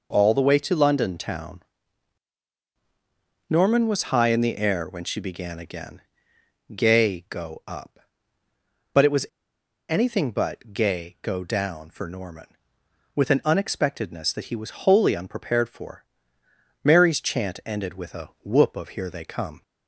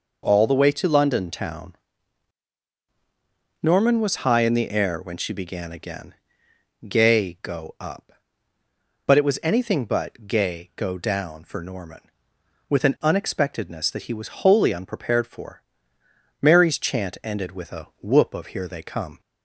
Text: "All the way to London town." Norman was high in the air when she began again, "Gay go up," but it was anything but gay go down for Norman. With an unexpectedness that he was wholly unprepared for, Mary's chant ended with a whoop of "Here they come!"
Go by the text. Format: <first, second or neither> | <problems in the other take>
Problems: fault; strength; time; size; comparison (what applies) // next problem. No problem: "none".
second | pauses between "was" and "anything"; noticeable; at 9.2 s; 0.63 s long